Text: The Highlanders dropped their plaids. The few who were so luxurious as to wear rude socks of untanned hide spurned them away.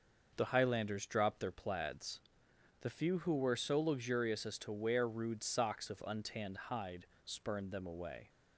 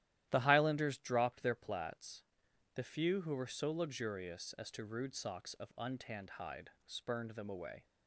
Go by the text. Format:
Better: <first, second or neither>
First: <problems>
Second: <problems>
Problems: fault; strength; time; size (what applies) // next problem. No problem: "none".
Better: first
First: pauses between "hide" and "spurned"; slight; at 7.0 s; 0.18 s long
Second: starts louder than the rest; strong; until 1.3 s; 13 dB // skips "wear"; at 4.8 s // pauses between "hide" and "spurned"; slight; at 6.7 s; 0.16 s long